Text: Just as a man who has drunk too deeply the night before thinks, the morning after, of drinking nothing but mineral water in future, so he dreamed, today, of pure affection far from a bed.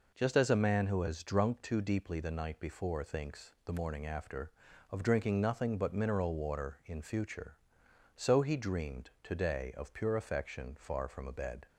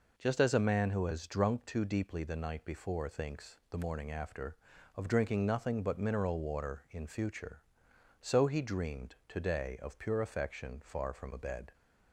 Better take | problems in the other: neither | none

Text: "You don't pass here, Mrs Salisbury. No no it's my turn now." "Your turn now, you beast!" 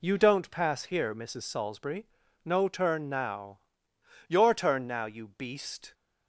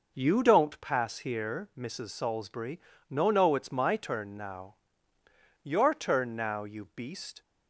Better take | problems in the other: second | skips "no it's my"; at 2.6 s

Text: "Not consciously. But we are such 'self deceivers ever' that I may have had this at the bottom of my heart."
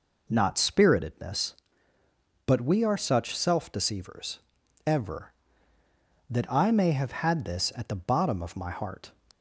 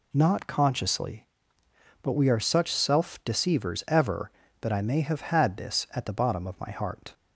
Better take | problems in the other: second | says "spiritedness" for "consciously"; at 0.5 s // pauses between "deceivers" and "ever"; noticeable; at 4.3 s; 0.46 s long

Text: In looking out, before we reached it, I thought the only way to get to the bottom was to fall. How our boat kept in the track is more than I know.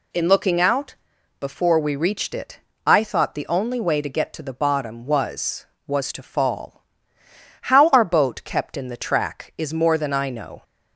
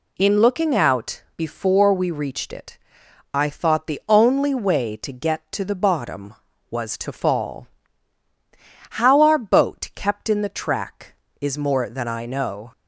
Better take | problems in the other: second | says "was" twice; at 5.8 s

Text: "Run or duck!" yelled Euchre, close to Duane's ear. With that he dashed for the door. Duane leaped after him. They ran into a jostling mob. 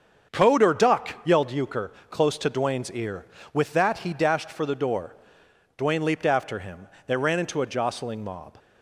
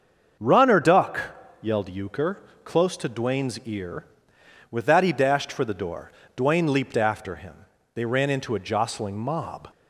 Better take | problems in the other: second | starts louder than the rest; strong; until 1.4 s; 7 dB; also in the second // says "Code" for "Run"; at 0.3 s

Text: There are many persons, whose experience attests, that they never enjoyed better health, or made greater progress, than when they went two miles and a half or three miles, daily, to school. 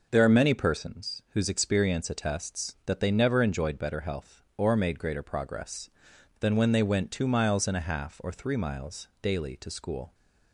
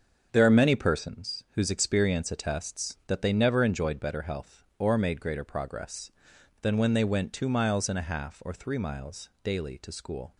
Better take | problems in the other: first | gets quieter; strong; throughout; 9.5 dB

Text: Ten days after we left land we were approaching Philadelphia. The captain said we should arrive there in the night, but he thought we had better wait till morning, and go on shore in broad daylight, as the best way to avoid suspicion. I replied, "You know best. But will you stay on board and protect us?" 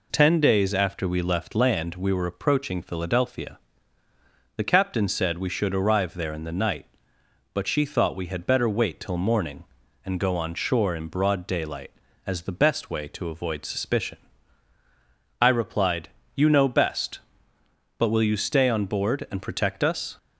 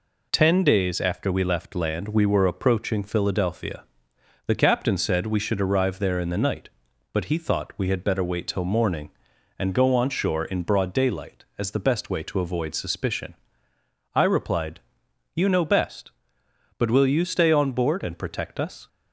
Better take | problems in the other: second | says "she" for "he"; at 7.6 s

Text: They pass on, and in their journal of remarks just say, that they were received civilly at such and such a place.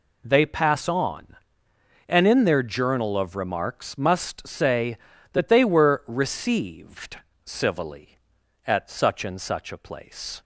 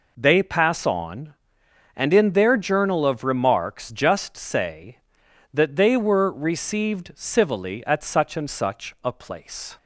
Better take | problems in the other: second | says "must" for "just"; at 3.9 s // pauses between "received" and "civilly"; slight; at 7.1 s; 0.26 s long

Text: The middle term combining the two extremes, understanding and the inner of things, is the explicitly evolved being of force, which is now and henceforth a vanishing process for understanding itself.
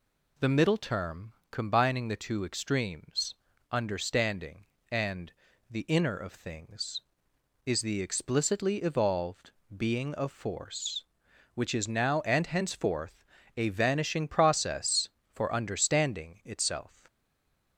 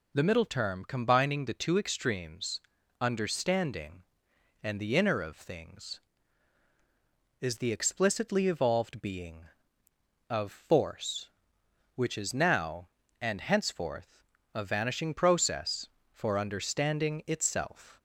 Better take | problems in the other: second | pauses between "term" and "combining"; slight; at 1.3 s; 0.18 s long // pauses between "and" and "the"; at 5.3 s; 0.38 s long // pauses between "evolved" and "being"; slight; at 9.5 s; 0.24 s long // pauses between "henceforth" and "a"; slight; at 13.2 s; 0.32 s long; slight in the second // stays silent after the last word; slight; from 17.0 s on; 0.7 s long

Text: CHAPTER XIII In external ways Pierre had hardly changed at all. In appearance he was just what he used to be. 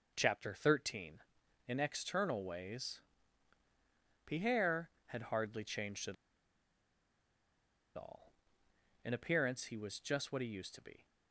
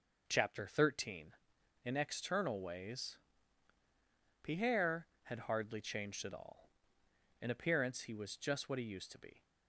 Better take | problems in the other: second | pauses between "ways" and "Pierre"; strong; at 3.0 s; 1.2 s long; strong in the second // pauses between "at" and "all"; strong; at 6.1 s; 1.8 s long

